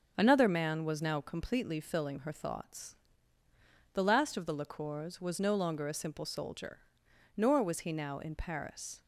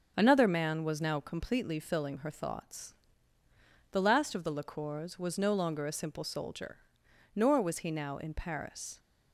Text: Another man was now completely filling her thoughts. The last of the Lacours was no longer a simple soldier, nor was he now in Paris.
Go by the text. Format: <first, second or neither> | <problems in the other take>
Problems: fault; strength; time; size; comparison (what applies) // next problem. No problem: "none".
neither | starts louder than the rest; the same in both